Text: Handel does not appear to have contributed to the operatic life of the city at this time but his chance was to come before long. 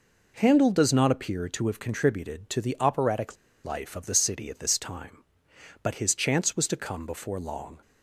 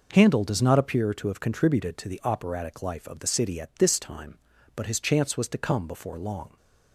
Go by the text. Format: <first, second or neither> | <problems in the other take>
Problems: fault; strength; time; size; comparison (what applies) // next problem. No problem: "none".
second | pauses between "operatic" and "life"; slight; at 3.3 s; 0.29 s long